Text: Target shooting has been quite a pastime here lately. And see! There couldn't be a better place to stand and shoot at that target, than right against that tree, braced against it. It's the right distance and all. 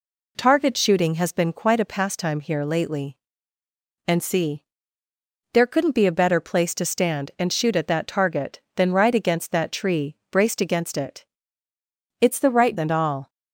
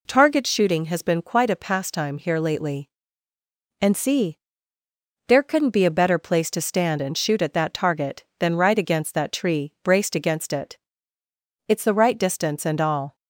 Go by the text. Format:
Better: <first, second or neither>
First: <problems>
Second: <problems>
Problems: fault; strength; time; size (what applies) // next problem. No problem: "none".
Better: second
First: skips "distance"; at 12.7 s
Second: none